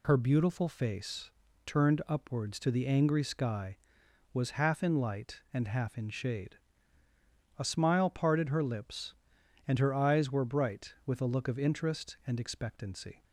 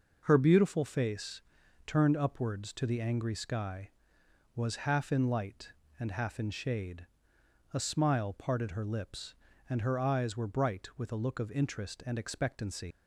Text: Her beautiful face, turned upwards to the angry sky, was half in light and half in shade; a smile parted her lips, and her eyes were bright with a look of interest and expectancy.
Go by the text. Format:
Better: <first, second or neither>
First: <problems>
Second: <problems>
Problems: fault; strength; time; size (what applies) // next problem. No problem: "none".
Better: first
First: none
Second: leaves "expectancy" unfinished; at 12.9 s; 130 ms